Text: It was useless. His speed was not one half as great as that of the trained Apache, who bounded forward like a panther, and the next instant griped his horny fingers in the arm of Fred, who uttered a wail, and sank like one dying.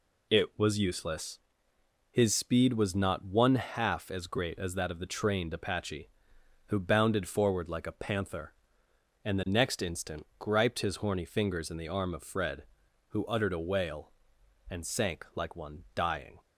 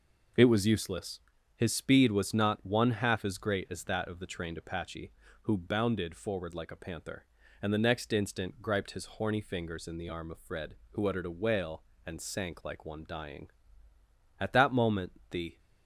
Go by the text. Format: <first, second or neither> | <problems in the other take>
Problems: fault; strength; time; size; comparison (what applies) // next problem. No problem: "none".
first | goes on to say "At that moment the"; noticeable; from 14.3 s on; 1.2 s long